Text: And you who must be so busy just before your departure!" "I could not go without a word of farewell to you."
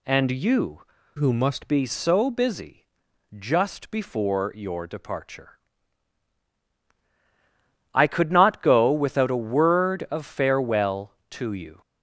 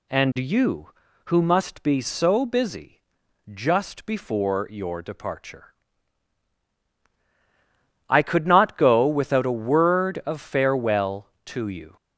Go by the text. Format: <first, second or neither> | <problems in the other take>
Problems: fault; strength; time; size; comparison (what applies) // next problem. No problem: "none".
second | changes voice from "who" to "must"; from 1.1 to 1.6 s; 0.5 s long // pauses between "busy" and "just"; noticeable; at 2.8 s; 0.52 s long; noticeable in the second